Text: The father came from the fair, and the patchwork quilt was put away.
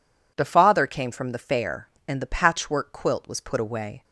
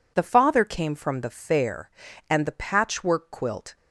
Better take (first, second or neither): first